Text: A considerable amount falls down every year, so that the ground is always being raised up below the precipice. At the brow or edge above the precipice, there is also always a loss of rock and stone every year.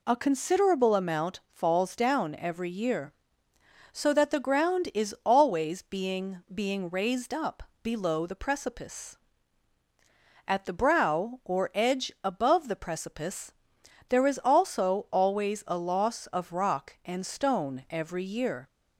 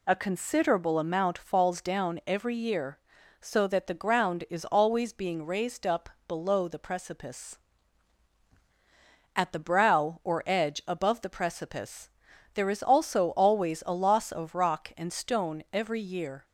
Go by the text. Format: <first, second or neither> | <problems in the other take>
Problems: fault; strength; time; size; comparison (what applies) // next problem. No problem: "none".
second | says "being" twice; at 6.5 s // pauses between "up" and "below"; slight; at 7.6 s; 0.22 s long; slight in the second